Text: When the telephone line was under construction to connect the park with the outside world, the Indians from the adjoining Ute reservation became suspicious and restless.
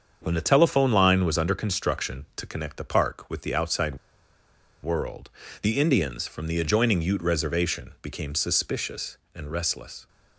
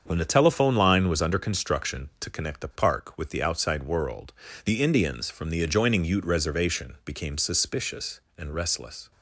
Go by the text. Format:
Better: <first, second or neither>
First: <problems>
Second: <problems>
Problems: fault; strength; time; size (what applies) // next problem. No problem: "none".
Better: second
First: starts louder than the rest; until 1.2 s; 7 dB // pauses between "outside" and "world"; noticeable; at 3.9 s; 0.86 s long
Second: starts louder than the rest; until 1.0 s; 7 dB